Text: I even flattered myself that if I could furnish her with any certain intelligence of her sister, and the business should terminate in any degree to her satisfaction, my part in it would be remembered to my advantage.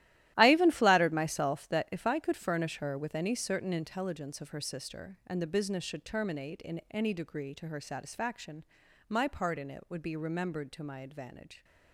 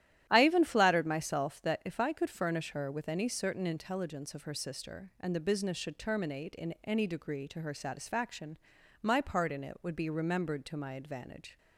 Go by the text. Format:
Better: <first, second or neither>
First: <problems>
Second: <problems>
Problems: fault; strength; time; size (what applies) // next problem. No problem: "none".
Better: second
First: gets quieter; strong; throughout; 13.5 dB // starts louder than the rest; strong; until 1.3 s; 14.5 dB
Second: starts louder than the rest; strong; until 1.3 s; 12.5 dB